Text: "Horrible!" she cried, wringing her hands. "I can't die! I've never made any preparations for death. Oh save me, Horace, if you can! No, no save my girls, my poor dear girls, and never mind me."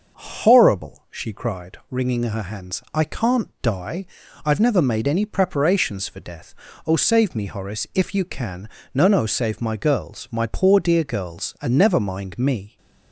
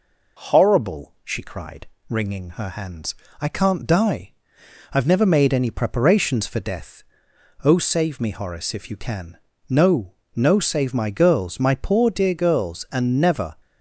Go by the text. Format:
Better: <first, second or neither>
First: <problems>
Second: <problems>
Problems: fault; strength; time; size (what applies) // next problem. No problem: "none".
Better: first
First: none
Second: stops before "mind me"; at 13.5 s